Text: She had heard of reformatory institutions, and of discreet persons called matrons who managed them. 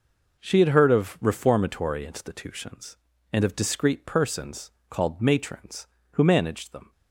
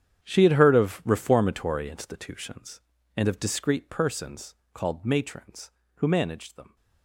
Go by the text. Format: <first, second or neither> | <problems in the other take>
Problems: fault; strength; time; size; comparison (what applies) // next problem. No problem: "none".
first | gets quieter; strong; throughout; 16 dB // pauses between "persons" and "called"; slight; at 4.5 s; 0.18 s long; slight in the first